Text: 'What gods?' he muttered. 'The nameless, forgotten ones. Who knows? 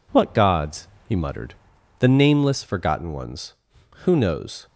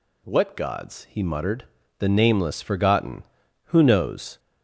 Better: first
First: none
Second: skips "ones"; at 3.4 s

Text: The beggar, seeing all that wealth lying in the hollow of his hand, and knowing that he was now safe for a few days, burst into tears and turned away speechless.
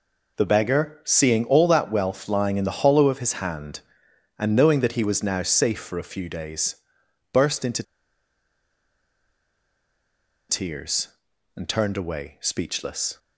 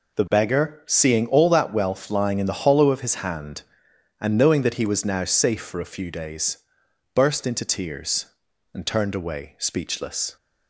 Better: second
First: pauses between "into" and "tears"; strong; at 7.8 s; 2.6 s long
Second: none

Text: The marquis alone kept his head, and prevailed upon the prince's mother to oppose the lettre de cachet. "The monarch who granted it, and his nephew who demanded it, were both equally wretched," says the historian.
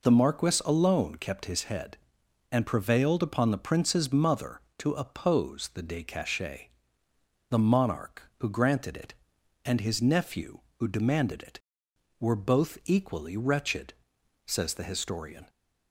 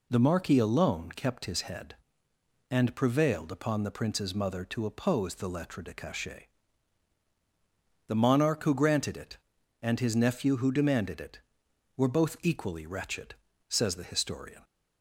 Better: second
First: skips "lettre"; at 5.8 s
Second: none

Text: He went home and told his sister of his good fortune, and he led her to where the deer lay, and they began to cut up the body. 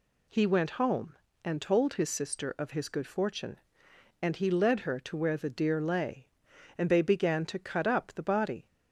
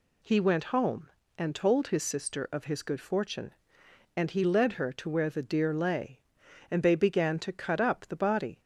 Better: neither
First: none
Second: none

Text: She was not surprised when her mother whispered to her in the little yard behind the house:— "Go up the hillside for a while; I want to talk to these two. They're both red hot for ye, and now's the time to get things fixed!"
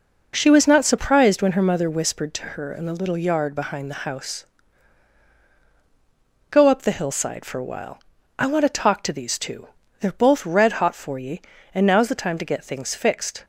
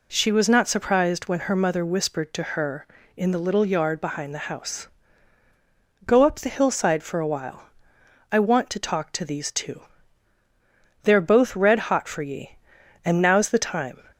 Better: first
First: none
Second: stops before "to get things fixed"; at 14.1 s

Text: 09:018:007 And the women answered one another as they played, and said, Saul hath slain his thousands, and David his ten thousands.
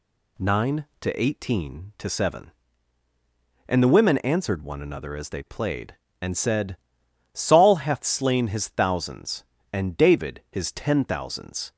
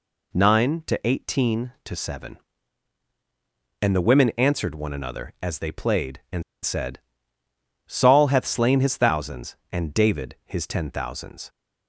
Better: first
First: none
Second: pauses between "and" and "said"; slight; at 6.4 s; 0.21 s long

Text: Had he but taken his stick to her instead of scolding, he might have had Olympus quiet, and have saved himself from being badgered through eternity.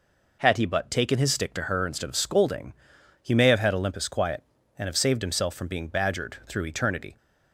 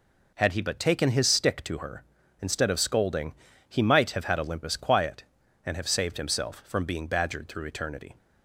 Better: second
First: says "may" for "might"; at 3.3 s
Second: none

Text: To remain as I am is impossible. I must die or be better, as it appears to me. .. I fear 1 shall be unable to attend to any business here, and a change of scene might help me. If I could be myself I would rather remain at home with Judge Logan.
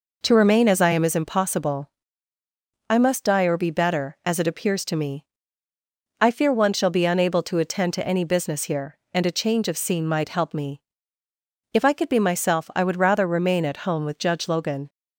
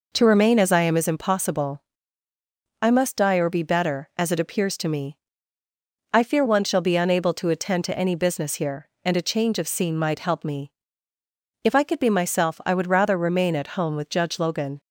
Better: neither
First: none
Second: none

